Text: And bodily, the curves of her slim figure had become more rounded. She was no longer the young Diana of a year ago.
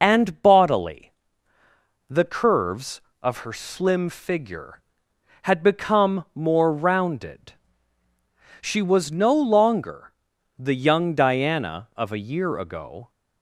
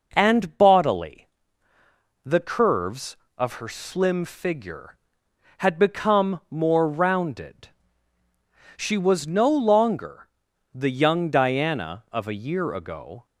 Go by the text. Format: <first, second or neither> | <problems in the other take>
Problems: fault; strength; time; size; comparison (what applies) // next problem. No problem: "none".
second | loses the start of "And"; at 0.0 s; 35 ms // pauses between "longer" and "the"; noticeable; at 10.1 s; 0.46 s long; noticeable in the second